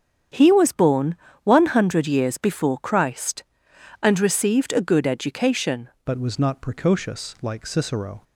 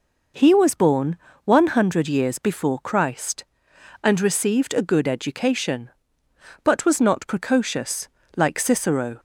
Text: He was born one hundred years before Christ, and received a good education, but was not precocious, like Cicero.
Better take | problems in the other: second | starts louder than the rest; strong; until 1.6 s; 8 dB // pauses between "born" and "one"; slight; at 1.1 s; 0.28 s long; slight in the second // changes voice at "but"; from 6.0 s on; 2.2 s long

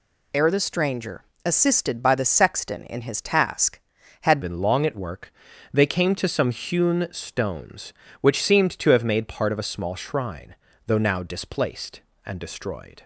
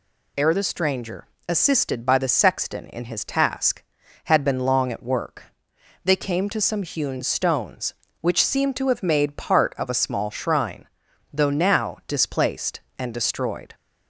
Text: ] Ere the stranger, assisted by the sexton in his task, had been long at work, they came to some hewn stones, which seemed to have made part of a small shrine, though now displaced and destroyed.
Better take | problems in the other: second | changes voice at "been"; from 4.4 s on; 8.6 s long

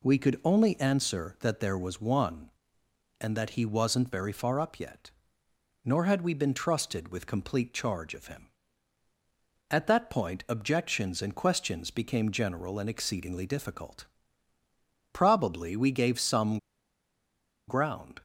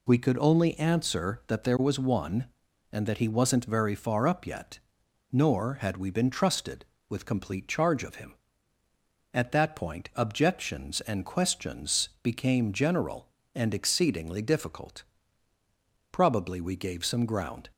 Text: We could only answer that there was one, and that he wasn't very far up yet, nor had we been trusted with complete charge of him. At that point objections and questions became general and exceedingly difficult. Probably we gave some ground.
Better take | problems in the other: second | pauses between "some" and "ground"; at 16.5 s; 1.0 s long

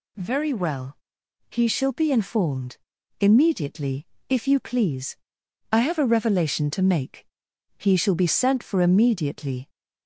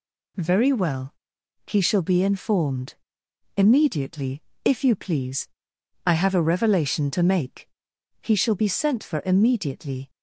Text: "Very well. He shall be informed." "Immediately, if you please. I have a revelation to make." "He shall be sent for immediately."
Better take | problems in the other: neither | none

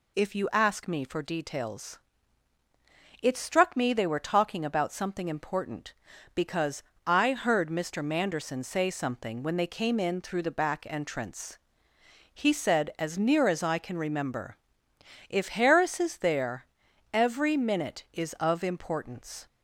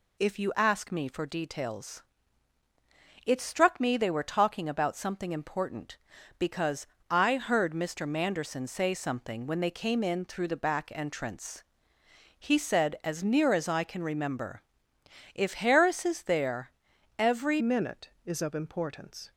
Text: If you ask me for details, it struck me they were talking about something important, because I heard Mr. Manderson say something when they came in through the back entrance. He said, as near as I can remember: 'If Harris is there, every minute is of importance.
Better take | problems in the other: first | pauses between "because" and "I"; slight; at 6.8 s; 0.24 s long; slight in the first // changes voice at "minute"; from 17.5 s on; 1.8 s long

